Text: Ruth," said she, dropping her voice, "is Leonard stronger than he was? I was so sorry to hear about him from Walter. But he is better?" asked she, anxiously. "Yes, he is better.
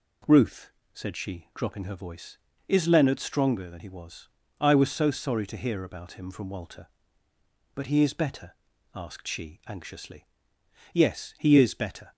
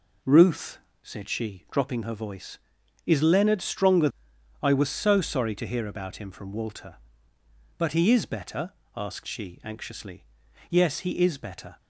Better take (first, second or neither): first